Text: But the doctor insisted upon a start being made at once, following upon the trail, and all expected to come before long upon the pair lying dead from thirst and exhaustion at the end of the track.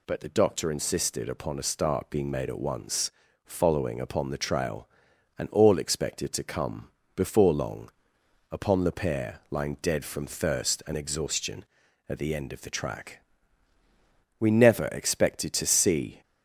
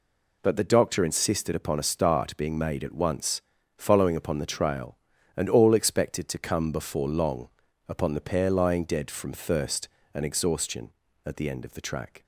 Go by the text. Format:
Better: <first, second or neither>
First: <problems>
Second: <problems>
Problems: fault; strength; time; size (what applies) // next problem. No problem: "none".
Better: second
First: pauses between "come" and "before"; slight; at 6.8 s; 0.26 s long // pauses between "long" and "upon"; noticeable; at 7.9 s; 0.60 s long // goes on to say "We never expected to see"; strong; from 14.4 s on; 1.8 s long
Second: pauses between "long" and "upon"; at 7.4 s; 0.38 s long